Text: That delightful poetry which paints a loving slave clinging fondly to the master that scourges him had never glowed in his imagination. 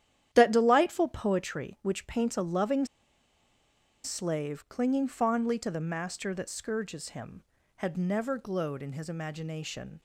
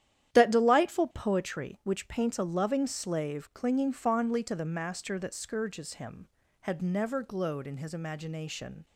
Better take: second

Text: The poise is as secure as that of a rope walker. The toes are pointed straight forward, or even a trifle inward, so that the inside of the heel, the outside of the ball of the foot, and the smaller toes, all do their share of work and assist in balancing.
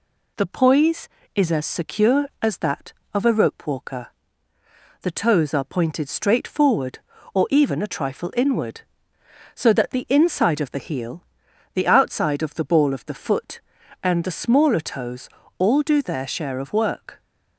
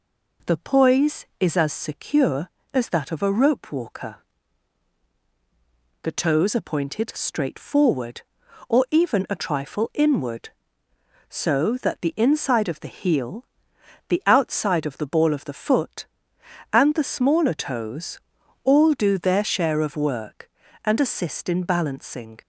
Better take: second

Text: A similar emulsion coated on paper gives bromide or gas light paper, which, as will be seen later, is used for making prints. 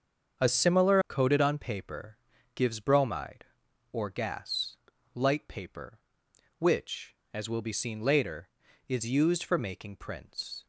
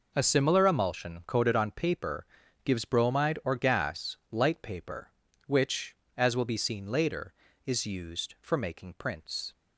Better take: second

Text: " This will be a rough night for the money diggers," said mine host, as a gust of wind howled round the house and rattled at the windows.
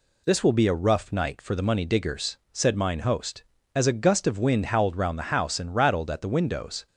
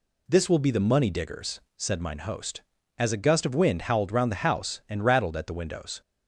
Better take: first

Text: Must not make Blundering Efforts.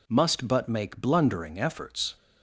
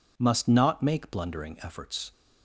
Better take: second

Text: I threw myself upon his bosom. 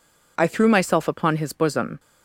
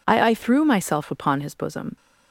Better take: first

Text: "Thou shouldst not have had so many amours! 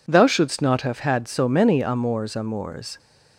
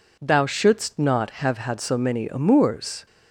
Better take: second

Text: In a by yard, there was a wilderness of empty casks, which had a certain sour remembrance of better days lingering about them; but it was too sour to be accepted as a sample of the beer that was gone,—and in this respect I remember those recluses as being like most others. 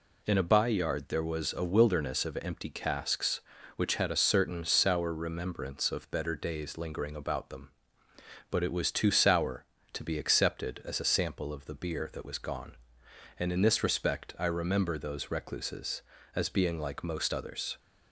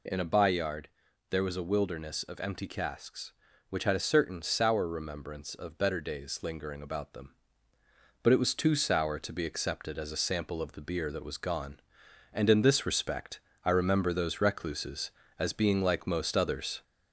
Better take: first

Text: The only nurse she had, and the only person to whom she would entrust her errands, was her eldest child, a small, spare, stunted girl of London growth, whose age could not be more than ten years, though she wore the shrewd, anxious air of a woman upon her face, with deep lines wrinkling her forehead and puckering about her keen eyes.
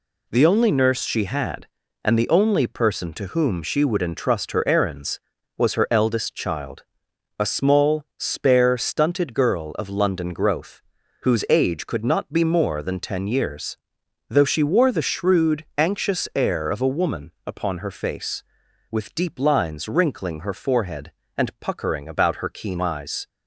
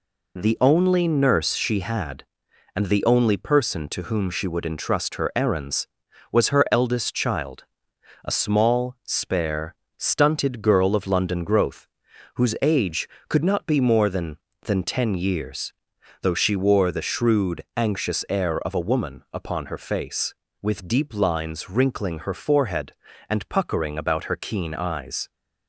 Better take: first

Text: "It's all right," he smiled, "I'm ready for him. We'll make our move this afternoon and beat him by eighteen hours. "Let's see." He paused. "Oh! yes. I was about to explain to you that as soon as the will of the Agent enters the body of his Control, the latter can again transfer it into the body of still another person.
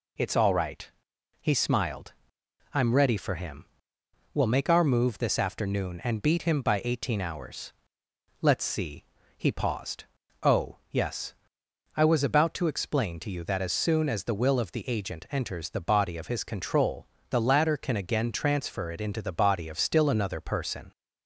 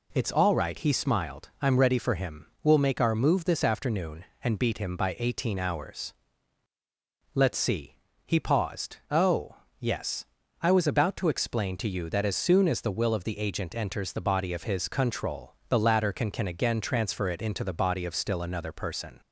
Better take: first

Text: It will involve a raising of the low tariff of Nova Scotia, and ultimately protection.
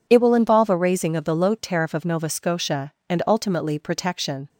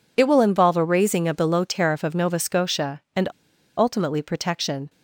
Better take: first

